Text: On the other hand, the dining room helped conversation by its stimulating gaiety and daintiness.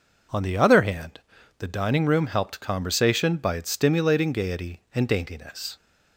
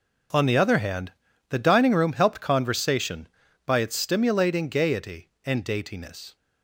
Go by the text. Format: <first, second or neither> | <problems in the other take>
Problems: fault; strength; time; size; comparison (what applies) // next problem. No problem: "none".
neither | none